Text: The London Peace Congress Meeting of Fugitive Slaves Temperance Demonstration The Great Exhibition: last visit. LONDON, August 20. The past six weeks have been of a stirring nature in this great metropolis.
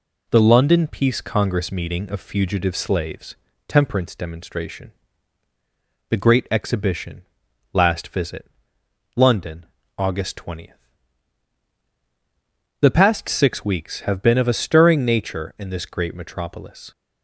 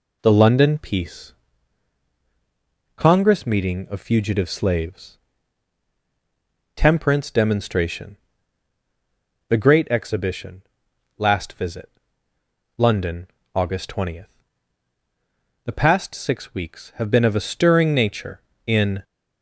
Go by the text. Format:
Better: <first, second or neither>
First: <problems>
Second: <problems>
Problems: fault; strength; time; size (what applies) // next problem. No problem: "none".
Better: first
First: pauses between "Slaves" and "Temperance"; slight; at 3.3 s; 0.32 s long // pauses between "Demonstration" and "The"; at 4.9 s; 1.1 s long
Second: pauses between "Peace" and "Congress"; strong; at 1.3 s; 1.6 s long // pauses between "Slaves" and "Temperance"; strong; at 5.1 s; 1.5 s long // pauses between "Demonstration" and "The"; strong; at 8.1 s; 1.3 s long // stops before "this great metropolis"; at 19.0 s